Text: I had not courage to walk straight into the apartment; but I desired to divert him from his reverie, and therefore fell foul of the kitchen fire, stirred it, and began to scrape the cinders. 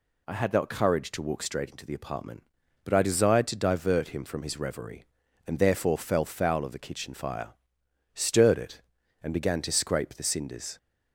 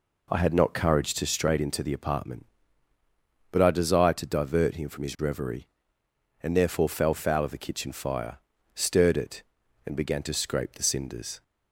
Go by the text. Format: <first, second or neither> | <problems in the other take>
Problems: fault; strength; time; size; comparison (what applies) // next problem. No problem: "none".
first | skips "walk"; at 1.2 s